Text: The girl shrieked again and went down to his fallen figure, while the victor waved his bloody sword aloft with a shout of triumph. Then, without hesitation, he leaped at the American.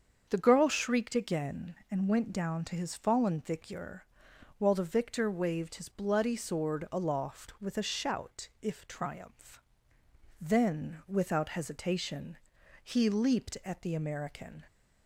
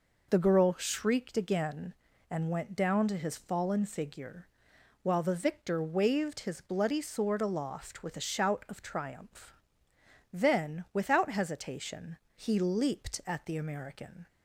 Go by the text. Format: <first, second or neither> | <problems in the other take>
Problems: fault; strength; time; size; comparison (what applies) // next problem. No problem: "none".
second | starts louder than the rest; until 1.3 s; 7 dB // says "if" for "of"; at 8.6 s